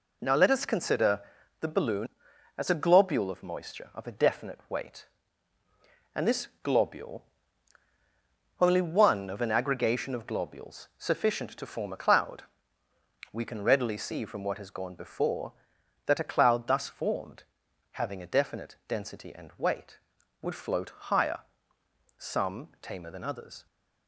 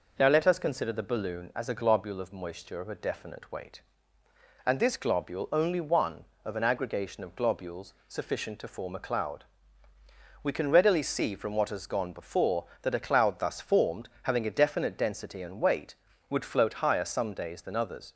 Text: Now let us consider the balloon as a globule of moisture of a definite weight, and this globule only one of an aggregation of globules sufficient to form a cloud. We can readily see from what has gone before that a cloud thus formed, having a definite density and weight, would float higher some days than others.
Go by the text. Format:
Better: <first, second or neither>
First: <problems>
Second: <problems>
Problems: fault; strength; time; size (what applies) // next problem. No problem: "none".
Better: second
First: pauses between "consider" and "the"; at 1.1 s; 0.40 s long // pauses between "this" and "globule"; slight; at 6.4 s; 0.16 s long // pauses between "globule" and "only"; strong; at 7.2 s; 1.3 s long // pauses between "higher" and "some"; noticeable; at 21.3 s; 0.78 s long // says "tamer" for "days"; at 22.7 s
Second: none